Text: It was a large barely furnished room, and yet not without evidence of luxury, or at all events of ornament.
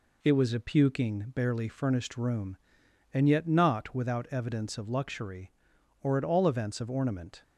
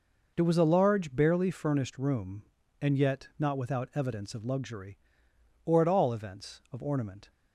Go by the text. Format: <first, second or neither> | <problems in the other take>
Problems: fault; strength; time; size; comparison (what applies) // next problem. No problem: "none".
second | says "puking" for "large"; at 0.6 s